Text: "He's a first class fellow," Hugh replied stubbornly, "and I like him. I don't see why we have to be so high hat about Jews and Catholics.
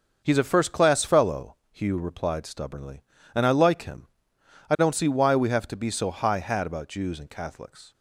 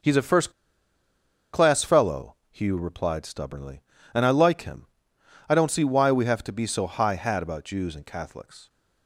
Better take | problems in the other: first | starts louder than the rest; until 2.0 s; 6.5 dB; also in the first // pauses between "first" and "class"; at 0.5 s; 1.0 s long

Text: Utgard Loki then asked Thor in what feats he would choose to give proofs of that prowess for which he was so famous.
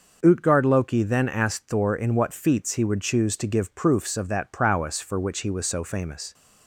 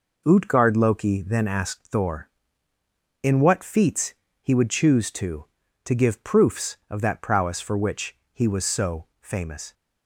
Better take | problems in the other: first | pauses between "feats" and "he"; slight; at 4.1 s; 0.28 s long // says "to" twice; at 5.8 s // pauses between "which" and "he"; slight; at 8.1 s; 0.16 s long

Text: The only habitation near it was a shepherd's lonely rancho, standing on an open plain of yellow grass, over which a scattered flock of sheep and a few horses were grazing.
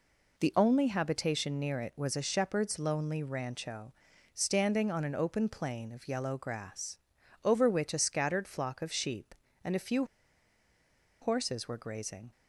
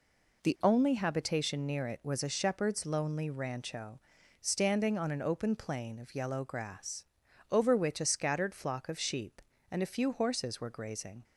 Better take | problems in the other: second | pauses between "few" and "horses"; at 10.0 s; 1.1 s long

